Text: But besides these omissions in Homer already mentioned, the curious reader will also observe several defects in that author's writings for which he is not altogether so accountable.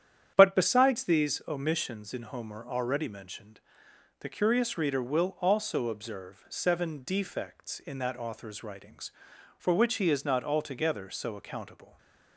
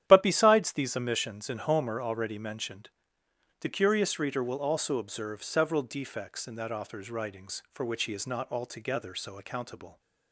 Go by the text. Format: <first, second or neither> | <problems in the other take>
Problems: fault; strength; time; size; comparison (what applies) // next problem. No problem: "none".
second | starts louder than the rest; strong; until 1.3 s; 9.5 dB; strong in the second // says "seven" for "several"; at 6.4 s // stays silent after the last word; slight; from 11.8 s on; 0.5 s long